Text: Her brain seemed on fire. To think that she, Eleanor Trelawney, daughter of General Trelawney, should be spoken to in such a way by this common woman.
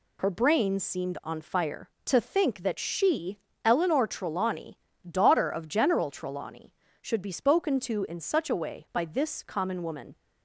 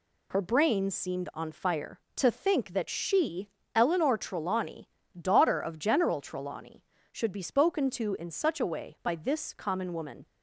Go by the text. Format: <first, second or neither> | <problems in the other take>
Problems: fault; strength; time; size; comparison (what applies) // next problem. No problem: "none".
neither | none